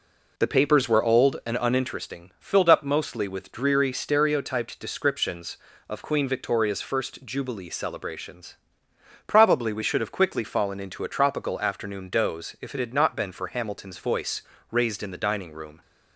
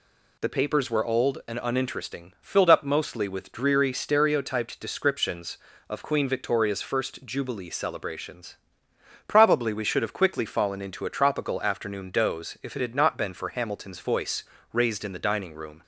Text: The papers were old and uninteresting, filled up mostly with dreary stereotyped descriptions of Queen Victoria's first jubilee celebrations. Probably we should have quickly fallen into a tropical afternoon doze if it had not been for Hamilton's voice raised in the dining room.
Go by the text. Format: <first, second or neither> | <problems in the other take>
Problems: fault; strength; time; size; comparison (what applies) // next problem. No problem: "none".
second | starts louder than the rest; until 1.8 s; 3.5 dB // pauses between "voice" and "raised"; slight; at 14.4 s; 0.30 s long; slight in the second